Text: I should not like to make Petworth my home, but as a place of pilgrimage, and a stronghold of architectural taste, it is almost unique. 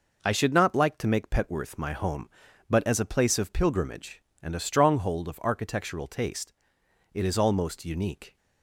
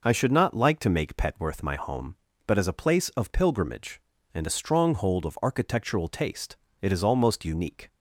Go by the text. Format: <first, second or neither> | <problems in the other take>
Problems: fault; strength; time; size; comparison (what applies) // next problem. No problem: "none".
neither | none